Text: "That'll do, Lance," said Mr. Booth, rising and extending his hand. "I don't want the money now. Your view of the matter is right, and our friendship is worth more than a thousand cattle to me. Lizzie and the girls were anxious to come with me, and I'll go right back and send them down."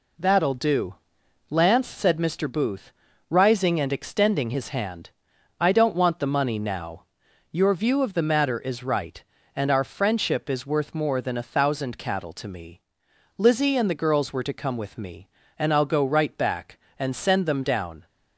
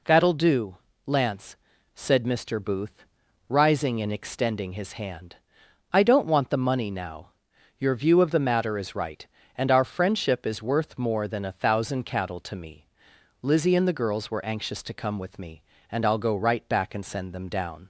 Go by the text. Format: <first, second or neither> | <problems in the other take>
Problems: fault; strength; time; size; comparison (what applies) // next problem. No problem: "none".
second | skips "anxious"; at 14.4 s